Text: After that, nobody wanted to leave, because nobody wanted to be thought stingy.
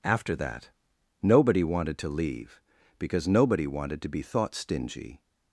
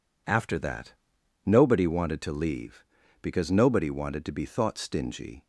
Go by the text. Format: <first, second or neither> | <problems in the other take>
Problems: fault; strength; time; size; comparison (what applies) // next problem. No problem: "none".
neither | none